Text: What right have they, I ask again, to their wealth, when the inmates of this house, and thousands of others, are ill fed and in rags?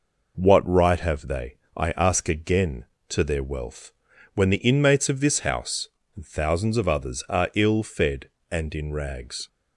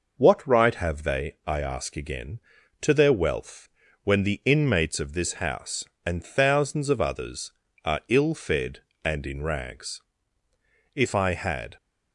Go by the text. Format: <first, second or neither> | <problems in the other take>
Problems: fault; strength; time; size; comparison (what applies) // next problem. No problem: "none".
first | goes on to say "If I had"; noticeable; from 10.9 s on; 0.82 s long